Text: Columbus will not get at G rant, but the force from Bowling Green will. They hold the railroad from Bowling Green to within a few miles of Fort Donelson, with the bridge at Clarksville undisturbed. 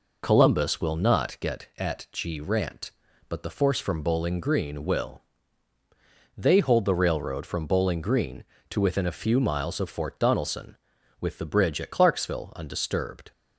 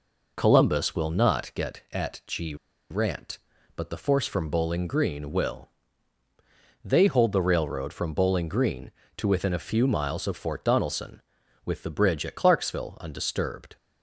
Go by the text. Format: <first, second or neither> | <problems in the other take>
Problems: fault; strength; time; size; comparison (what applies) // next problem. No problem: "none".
first | pauses between "G" and "rant"; slight; at 2.5 s; 0.35 s long